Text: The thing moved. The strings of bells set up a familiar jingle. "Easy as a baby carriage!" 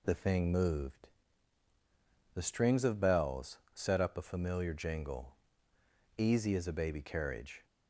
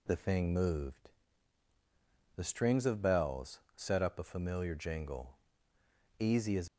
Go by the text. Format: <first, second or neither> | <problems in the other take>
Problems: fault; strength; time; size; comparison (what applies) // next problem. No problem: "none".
first | pauses between "bells" and "set"; slight; at 3.5 s; 0.16 s long; slight in the first // stops before "a baby carriage"; at 6.6 s